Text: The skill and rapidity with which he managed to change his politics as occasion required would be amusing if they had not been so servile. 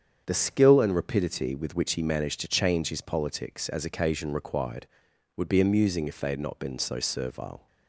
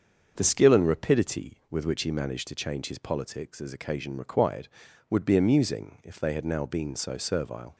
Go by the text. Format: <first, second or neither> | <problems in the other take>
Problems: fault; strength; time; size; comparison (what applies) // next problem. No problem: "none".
first | starts louder than the rest; until 1.3 s; 6.5 dB; strong in the first // says "now" for "not"; at 6.4 s